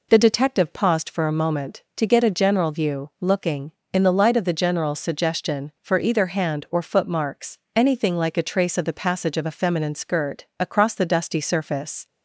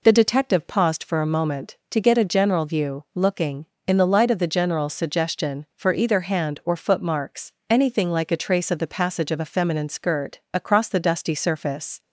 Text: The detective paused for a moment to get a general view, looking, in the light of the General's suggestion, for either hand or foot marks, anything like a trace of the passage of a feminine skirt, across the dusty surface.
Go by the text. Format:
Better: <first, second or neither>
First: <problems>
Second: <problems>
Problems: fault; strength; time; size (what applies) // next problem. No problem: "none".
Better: neither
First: none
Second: none